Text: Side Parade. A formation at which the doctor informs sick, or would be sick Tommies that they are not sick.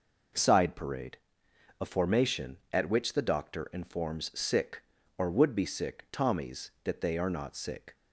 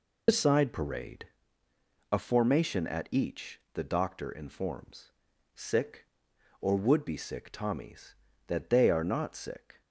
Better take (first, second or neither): first